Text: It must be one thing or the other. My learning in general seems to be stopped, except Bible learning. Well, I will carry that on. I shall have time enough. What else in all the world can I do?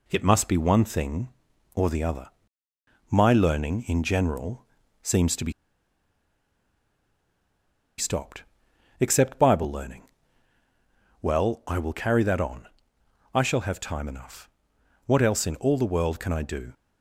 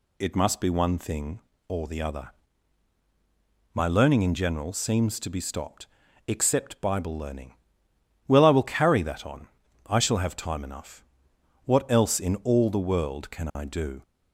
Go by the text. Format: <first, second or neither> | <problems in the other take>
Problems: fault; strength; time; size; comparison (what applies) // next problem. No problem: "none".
second | pauses between "general" and "seems"; at 4.6 s; 0.38 s long // pauses between "be" and "stopped"; strong; at 5.5 s; 2.4 s long